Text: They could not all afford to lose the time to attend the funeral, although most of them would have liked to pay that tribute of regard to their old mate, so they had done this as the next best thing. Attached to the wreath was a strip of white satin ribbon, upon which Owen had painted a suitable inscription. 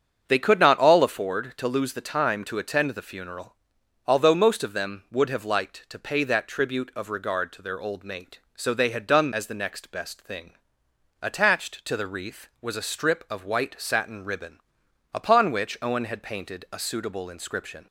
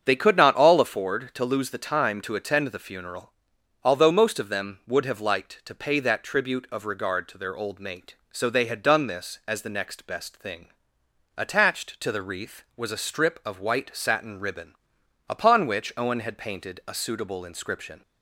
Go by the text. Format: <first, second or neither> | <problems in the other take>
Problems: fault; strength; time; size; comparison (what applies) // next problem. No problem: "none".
second | starts louder than the rest; until 1.2 s; 7 dB; also in the second // skips "this"; at 9.3 s